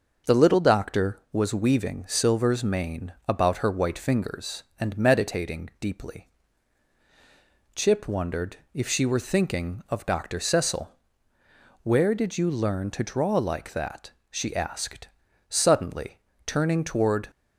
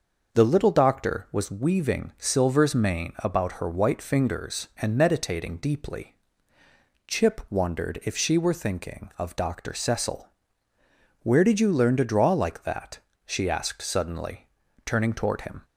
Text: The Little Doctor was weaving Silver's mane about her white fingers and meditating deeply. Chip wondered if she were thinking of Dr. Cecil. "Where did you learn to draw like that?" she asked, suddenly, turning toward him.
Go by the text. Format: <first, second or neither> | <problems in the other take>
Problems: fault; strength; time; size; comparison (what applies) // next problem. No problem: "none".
second | starts louder than the rest; until 1.3 s; 6.5 dB; also in the second // pauses between "wondered" and "if"; slight; at 8.5 s; 0.16 s long // stops before "him"; at 17.3 s